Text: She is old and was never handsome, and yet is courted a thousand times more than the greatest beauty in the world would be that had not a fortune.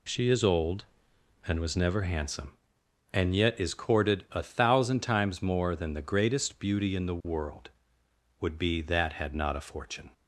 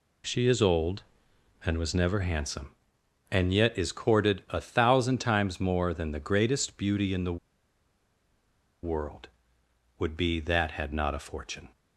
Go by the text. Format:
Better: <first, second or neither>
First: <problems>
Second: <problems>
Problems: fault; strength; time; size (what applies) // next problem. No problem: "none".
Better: first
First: none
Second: pauses between "the" and "world"; strong; at 7.3 s; 1.4 s long